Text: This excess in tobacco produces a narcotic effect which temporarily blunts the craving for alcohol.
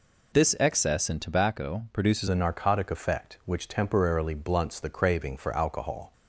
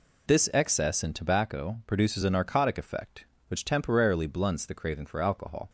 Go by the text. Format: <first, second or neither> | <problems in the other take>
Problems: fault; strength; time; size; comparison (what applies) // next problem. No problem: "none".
second | changes voice at "a"; from 2.2 s on; 3.9 s long